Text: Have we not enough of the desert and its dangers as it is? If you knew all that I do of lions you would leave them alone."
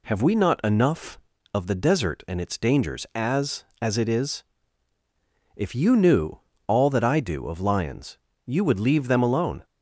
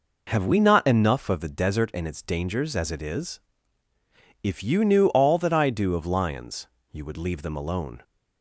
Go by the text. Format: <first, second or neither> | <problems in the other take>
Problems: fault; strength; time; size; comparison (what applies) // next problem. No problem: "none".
second | says "as" twice; at 3.8 s // pauses between "knew" and "all"; slight; at 6.4 s; 0.26 s long // pauses between "lions" and "you"; slight; at 8.1 s; 0.26 s long; slight in the second